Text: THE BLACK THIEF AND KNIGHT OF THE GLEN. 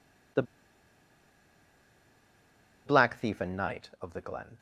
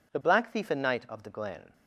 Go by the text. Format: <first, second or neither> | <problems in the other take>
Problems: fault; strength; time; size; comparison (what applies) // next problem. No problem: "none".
second | pauses between "THE" and "BLACK"; strong; at 0.4 s; 2.4 s long